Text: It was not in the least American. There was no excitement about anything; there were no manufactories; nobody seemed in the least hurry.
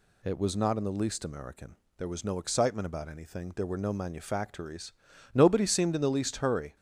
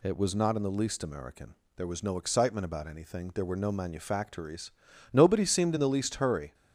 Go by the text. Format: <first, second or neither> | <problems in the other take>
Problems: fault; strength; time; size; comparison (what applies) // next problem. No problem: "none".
neither | none